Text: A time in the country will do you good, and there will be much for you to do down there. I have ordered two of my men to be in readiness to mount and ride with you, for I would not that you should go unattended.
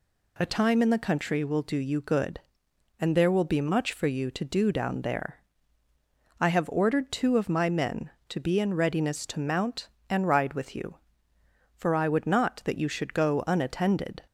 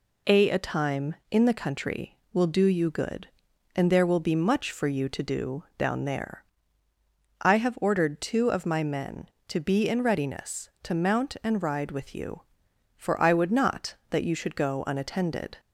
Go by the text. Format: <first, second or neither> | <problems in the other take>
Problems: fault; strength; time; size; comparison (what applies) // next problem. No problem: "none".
first | says "A" twice; at 0.5 s // pauses between "do" and "down"; slight; at 5.6 s; 0.16 s long